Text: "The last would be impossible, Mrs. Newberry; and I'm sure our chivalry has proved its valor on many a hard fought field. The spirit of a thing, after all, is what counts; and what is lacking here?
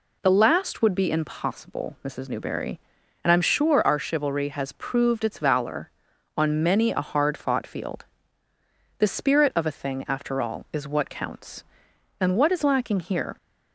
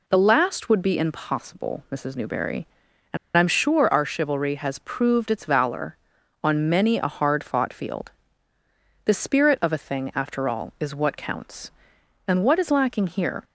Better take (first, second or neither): first